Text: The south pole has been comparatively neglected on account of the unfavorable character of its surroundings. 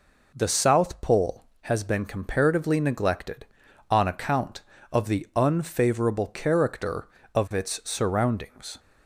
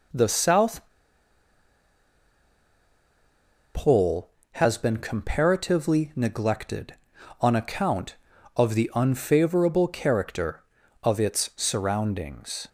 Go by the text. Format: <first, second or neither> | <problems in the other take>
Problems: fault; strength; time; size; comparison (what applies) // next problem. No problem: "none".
first | pauses between "south" and "pole"; strong; at 0.8 s; 2.8 s long